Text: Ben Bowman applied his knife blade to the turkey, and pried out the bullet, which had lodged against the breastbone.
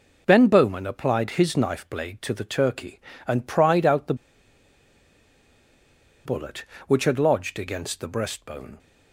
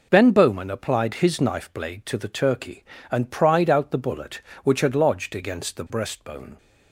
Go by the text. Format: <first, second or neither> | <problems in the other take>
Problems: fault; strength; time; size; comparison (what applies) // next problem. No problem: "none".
second | pauses between "the" and "bullet"; strong; at 4.1 s; 2.1 s long